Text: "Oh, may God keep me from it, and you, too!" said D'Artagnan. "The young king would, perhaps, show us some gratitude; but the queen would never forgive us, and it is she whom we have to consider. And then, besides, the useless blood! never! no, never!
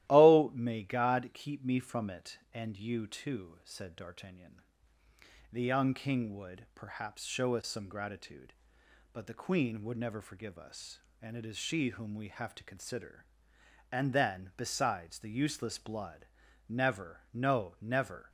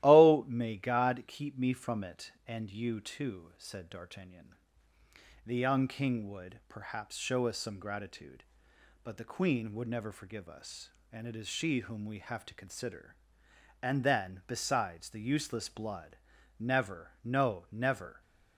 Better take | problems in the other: neither | starts louder than the rest; strong; the same in both

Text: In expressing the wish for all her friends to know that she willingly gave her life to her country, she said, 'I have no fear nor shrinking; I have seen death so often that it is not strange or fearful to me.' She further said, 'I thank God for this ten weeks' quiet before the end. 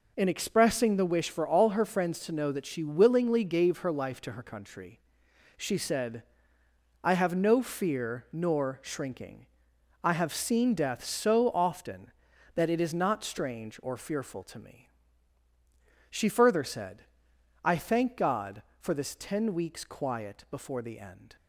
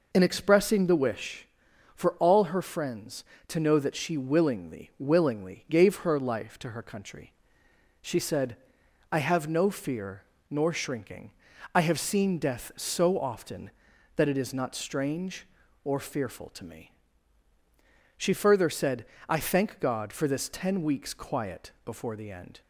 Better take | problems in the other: first | says "willingly" twice; at 4.9 s // pauses between "fear" and "nor"; slight; at 10.2 s; 0.28 s long

